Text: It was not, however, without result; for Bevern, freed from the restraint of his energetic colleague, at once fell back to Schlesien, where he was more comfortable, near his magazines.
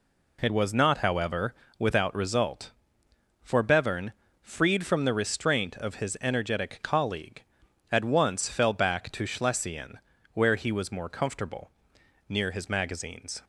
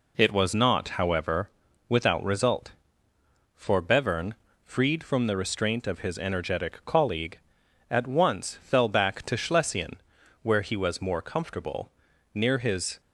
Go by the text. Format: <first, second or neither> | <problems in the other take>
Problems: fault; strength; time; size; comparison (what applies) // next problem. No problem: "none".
first | stops before "magazines"; at 13.0 s